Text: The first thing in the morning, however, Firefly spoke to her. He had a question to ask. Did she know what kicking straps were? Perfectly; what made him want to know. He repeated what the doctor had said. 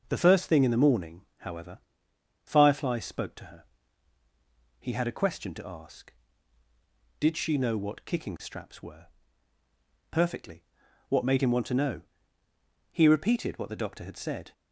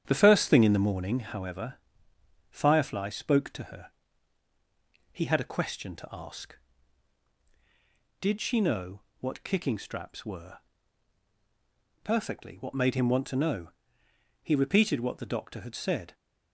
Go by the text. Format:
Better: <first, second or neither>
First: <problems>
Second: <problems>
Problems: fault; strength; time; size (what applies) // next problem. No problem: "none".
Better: first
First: none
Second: starts louder than the rest; strong; until 1.5 s; 9 dB // pauses between "know" and "what"; slight; at 8.9 s; 0.22 s long